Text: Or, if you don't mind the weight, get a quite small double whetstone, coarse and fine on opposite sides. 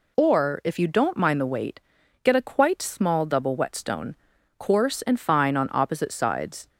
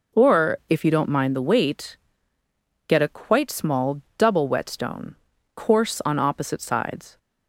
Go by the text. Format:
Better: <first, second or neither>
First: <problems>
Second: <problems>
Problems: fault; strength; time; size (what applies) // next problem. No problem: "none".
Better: first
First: none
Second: pauses between "small" and "double"; slight; at 3.9 s; 0.18 s long // skips "and fine"; at 6.0 s